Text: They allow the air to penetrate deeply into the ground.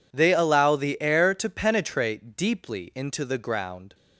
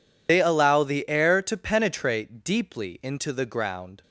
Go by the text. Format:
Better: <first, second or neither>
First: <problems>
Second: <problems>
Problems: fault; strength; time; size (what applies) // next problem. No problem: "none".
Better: first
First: none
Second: loses the start of "They"; at 0.2 s; 95 ms